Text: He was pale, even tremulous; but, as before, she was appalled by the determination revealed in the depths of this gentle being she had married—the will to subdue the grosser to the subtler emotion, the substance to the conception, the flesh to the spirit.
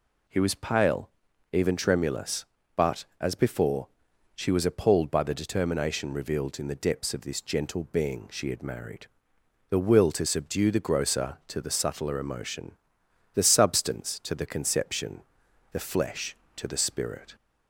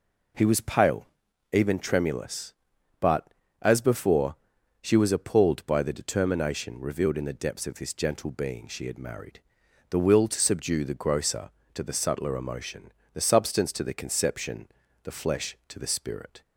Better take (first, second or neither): neither